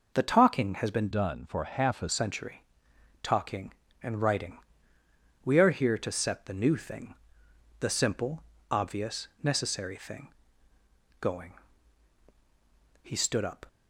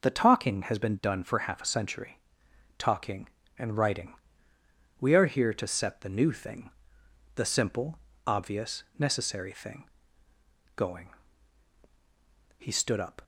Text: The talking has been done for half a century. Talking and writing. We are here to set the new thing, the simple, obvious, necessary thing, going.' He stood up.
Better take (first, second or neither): second